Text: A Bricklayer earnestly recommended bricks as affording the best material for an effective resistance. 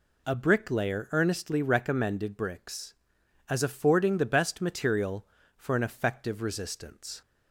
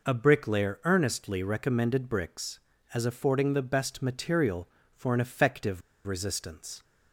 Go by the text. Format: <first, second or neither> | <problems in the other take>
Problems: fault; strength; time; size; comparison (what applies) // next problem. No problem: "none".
first | pauses between "effective" and "resistance"; slight; at 5.8 s; 0.25 s long